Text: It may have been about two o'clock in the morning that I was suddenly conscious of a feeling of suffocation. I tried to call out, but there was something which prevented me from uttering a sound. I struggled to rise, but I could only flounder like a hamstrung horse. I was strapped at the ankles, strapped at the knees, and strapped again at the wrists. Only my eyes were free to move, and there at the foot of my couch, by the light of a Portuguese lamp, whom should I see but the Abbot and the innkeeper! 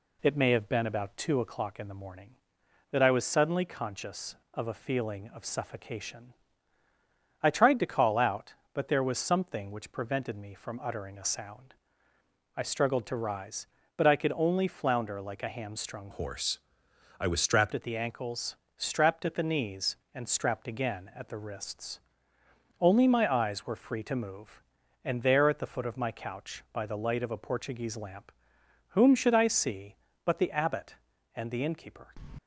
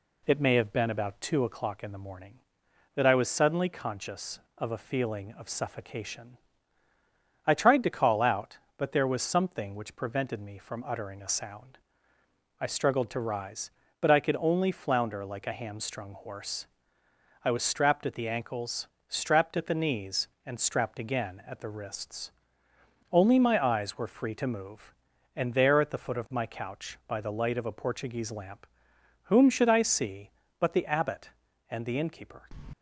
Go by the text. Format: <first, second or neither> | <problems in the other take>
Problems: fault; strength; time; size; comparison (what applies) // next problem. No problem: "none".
second | changes voice from "horse" to "strapped"; from 16.1 to 17.7 s; 1.6 s long